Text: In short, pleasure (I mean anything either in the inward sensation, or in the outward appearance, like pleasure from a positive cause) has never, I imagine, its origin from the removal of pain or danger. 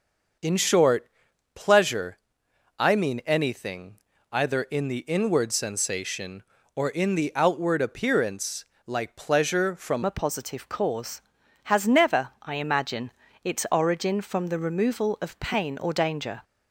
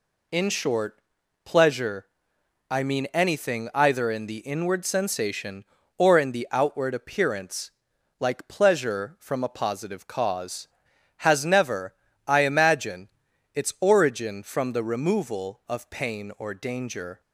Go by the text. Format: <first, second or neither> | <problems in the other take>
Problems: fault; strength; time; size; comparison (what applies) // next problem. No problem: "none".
second | starts louder than the rest; noticeable; until 1.8 s; 6 dB // pauses between "anything" and "either"; slight; at 3.9 s; 0.34 s long // changes voice at "a"; from 10.0 s on; 6.4 s long